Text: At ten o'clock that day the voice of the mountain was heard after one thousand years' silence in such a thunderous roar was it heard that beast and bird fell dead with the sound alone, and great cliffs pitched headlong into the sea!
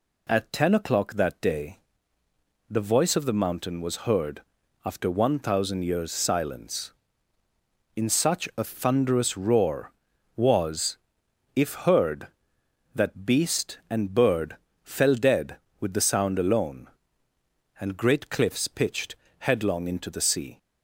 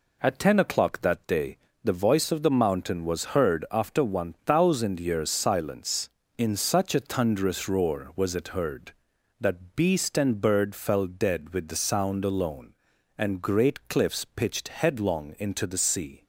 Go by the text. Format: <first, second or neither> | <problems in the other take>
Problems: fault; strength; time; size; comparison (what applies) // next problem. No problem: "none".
second | pauses between "day" and "the"; noticeable; at 1.7 s; 0.92 s long; slight in the second // pauses between "heard" and "after"; at 4.4 s; 0.42 s long // says "if" for "it"; at 11.5 s // pauses between "bird" and "fell"; slight; at 14.5 s; 0.26 s long // pauses between "pitched" and "headlong"; slight; at 19.1 s; 0.24 s long